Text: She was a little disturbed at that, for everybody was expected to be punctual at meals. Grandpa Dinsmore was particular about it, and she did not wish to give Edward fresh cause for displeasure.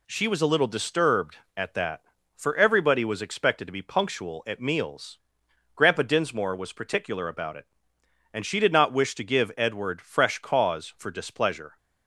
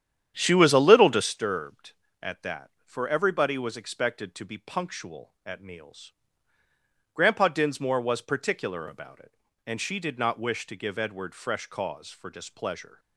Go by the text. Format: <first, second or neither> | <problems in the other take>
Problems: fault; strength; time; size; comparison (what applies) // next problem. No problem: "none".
first | starts louder than the rest; strong; until 1.3 s; 9.5 dB